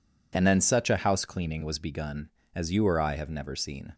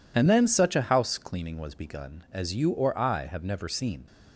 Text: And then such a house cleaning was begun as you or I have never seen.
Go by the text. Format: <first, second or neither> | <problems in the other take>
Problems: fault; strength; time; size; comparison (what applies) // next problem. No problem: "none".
neither | none